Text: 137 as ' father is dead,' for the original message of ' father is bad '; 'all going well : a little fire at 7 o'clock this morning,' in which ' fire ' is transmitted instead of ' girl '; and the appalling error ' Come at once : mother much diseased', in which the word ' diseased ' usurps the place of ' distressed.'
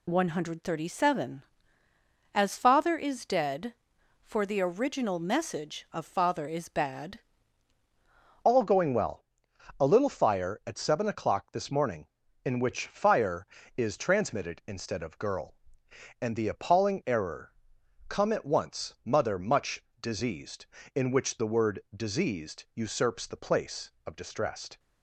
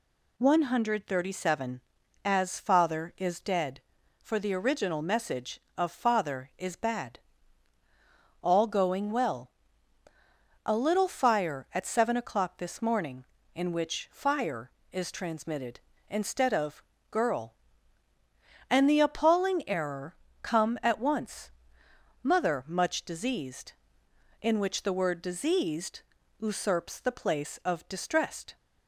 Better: second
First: changes voice at "all"; from 8.4 s on; 16.3 s long // pauses between "much" and "diseased"; slight; at 19.8 s; 0.16 s long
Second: none

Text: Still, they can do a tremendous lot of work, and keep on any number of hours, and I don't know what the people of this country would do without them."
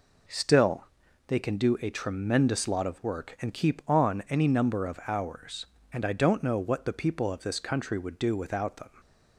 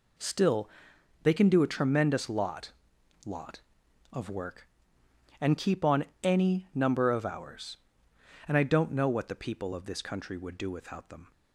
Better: first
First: none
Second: says "lot" twice; at 3.2 s // pauses between "on" and "any"; slight; at 6.0 s; 0.18 s long

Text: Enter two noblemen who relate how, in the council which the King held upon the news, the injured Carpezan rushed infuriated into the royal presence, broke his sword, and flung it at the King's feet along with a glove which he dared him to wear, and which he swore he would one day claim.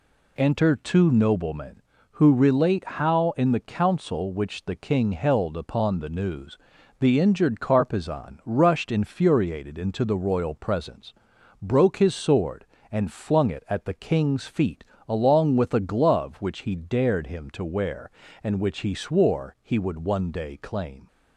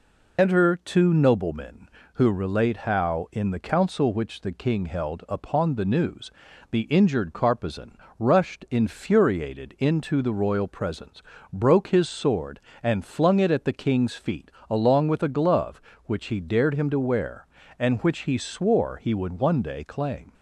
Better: first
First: pauses between "feet" and "along"; slight; at 14.8 s; 0.26 s long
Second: loses the start of "Enter"; at 0.3 s; 55 ms // pauses between "Carpezan" and "rushed"; slight; at 7.9 s; 0.22 s long // pauses between "feet" and "along"; slight; at 14.5 s; 0.18 s long

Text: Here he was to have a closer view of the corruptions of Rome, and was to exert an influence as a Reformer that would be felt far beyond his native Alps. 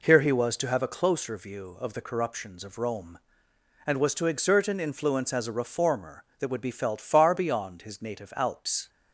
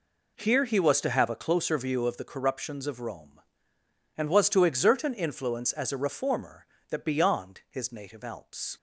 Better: first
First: none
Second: skips "would be felt far"; at 7.0 s

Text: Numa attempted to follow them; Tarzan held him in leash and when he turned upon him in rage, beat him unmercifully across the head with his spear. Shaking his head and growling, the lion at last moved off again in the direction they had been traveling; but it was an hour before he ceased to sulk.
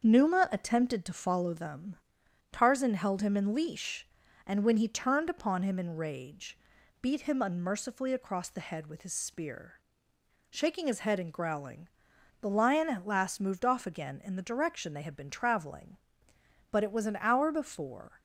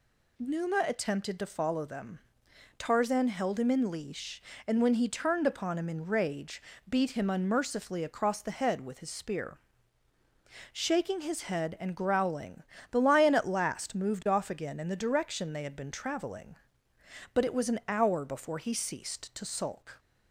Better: second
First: starts louder than the rest; until 1.0 s; 6.5 dB // stops before "he ceased to sulk"; at 18.1 s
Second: none

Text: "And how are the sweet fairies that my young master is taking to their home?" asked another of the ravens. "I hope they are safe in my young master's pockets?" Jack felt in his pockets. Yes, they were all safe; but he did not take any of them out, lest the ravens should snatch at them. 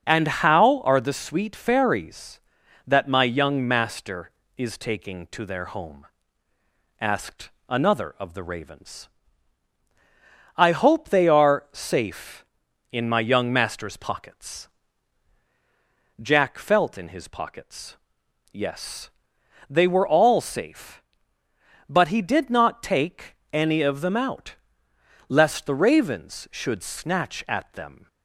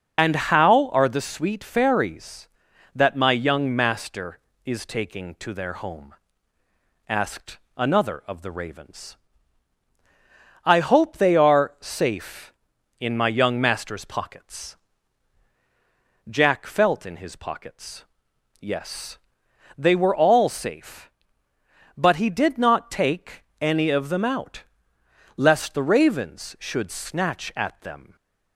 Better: first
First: pauses between "asked" and "another"; slight; at 7.5 s; 0.18 s long // pauses between "take" and "any"; slight; at 23.3 s; 0.16 s long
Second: loses the start of "And"; at 0.1 s; 50 ms // pauses between "asked" and "another"; slight; at 7.5 s; 0.18 s long // pauses between "take" and "any"; slight; at 23.4 s; 0.16 s long

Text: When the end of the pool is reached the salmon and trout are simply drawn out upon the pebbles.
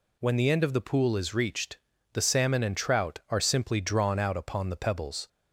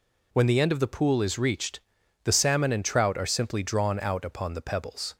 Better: neither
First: pauses between "reached" and "the"; slight; at 1.7 s; 0.36 s long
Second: pauses between "reached" and "the"; at 1.8 s; 0.42 s long

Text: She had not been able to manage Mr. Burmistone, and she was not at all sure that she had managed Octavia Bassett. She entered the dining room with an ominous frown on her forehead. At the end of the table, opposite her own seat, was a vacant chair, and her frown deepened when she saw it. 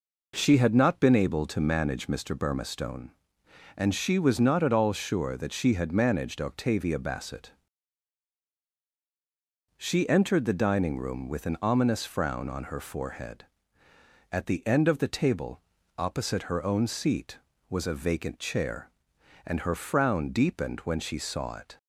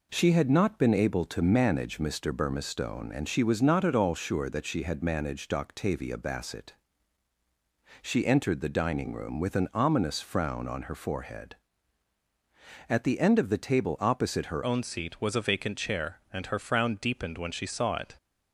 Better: first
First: none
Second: changes voice at "own"; from 14.6 s on; 3.5 s long

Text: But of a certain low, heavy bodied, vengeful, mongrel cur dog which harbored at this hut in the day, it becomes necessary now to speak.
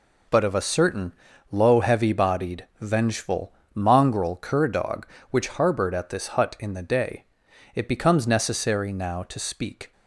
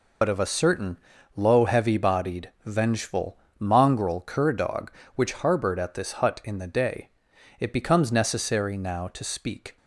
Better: first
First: pauses between "certain" and "low"; slight; at 1.1 s; 0.36 s long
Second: loses the start of "But"; at 0.2 s; 70 ms // pauses between "certain" and "low"; slight; at 0.9 s; 0.36 s long

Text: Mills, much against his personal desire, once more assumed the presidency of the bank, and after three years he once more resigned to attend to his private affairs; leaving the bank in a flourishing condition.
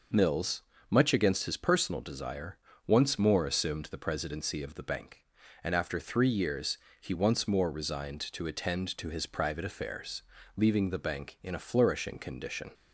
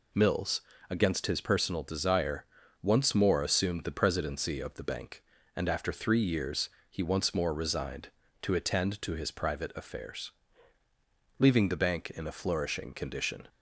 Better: first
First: pauses between "years" and "he"; slight; at 6.7 s; 0.22 s long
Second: skips "much"; at 0.7 s // pauses between "years" and "he"; slight; at 6.6 s; 0.22 s long

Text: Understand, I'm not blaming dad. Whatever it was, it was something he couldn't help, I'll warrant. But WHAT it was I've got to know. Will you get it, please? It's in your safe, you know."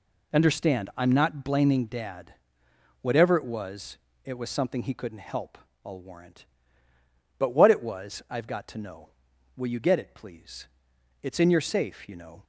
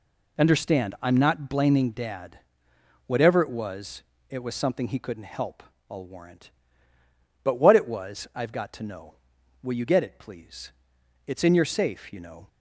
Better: neither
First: none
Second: none

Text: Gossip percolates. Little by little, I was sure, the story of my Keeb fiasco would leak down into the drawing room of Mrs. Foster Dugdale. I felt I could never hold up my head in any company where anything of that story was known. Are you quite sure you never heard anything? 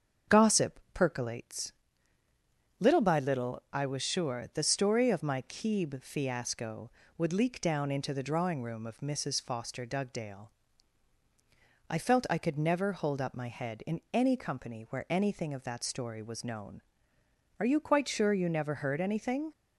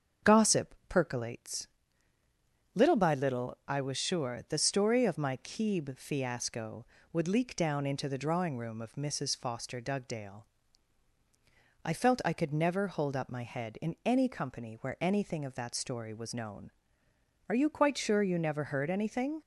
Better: neither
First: starts louder than the rest; strong; until 1.4 s; 7 dB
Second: starts louder than the rest; strong; until 1.3 s; 7 dB

